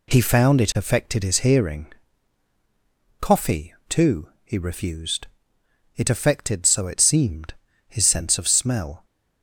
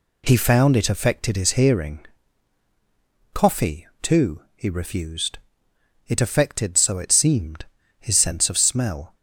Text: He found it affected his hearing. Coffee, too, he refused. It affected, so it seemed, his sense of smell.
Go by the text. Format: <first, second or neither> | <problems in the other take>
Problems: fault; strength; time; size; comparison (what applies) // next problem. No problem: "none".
neither | none